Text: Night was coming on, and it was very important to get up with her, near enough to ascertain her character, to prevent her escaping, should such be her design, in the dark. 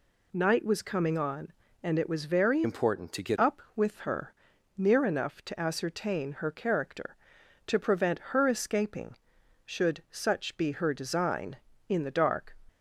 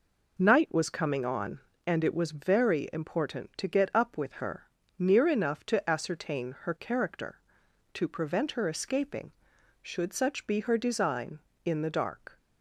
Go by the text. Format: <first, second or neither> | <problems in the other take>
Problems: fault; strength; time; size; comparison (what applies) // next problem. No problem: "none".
second | changes voice from "important" to "get"; from 2.6 to 3.3 s; 0.7 s long